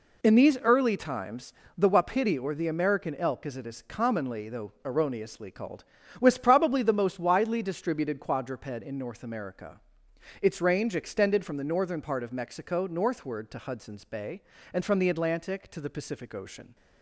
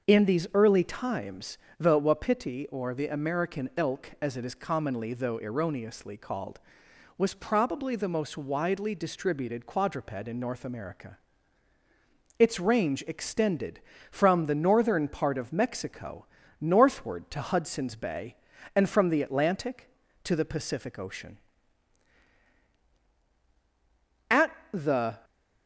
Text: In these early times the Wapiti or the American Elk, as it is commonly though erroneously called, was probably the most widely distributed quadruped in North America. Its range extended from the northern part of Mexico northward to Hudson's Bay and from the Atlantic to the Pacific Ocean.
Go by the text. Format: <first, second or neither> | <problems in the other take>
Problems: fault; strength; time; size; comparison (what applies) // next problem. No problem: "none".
first | starts louder than the rest; until 1.1 s; 6.5 dB // pauses between "times" and "the"; slight; at 1.5 s; 0.24 s long; slight in the first // pauses between "Mexico" and "northward"; slight; at 16.2 s; 0.34 s long // goes on to say "At the"; noticeable; from 24.2 s on; 0.94 s long